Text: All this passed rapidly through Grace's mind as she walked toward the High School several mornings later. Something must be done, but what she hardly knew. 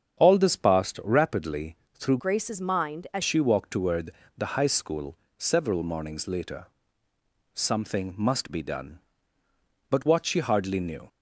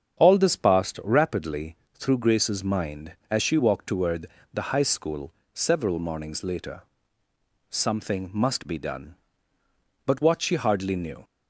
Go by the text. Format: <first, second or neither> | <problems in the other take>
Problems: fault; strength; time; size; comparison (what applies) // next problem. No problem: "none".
second | starts louder than the rest; strong; until 1.2 s; 8 dB; strong in the second // pauses between "rapidly" and "through"; slight; at 1.7 s; 0.18 s long; slight in the second // changes voice from "Grace's" to "as"; from 2.1 to 3.2 s; 1.1 s long // pauses between "toward" and "the"; slight; at 4.1 s; 0.24 s long; slight in the second // pauses between "School" and "several"; slight; at 5.1 s; 0.22 s long; slight in the second